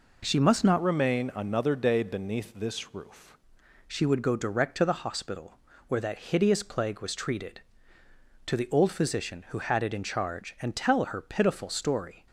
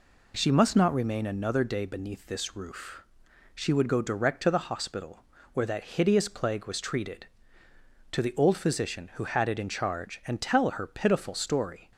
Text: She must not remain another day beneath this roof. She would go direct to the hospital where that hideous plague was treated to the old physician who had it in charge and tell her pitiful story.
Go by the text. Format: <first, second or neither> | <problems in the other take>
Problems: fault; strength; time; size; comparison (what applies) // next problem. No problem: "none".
second | changes voice from "remain" to "roof"; from 0.8 to 3.3 s; 2.5 s long // pauses between "hospital" and "where"; slight; at 5.5 s; 0.32 s long; slight in the second